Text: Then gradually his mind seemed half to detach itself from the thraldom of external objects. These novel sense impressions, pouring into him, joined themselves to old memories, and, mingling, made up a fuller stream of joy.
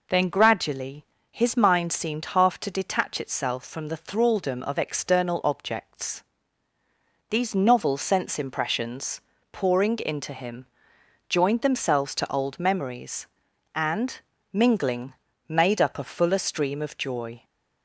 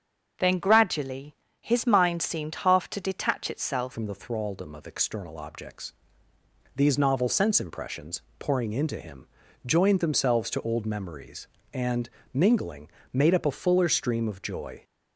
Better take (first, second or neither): first